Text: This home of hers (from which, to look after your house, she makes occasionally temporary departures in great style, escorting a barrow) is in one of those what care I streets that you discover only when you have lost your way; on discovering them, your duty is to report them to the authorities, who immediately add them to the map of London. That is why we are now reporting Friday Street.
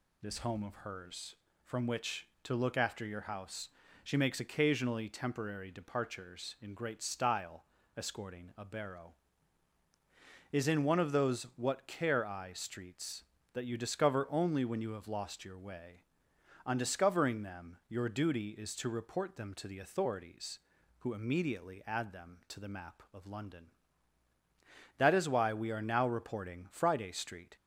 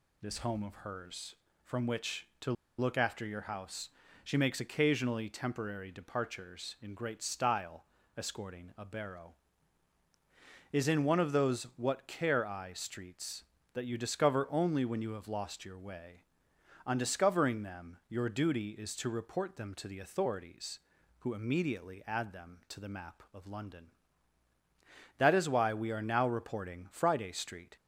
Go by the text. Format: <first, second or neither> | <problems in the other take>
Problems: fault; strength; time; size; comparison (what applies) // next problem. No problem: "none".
first | pauses between "to" and "look"; slight; at 2.5 s; 0.26 s long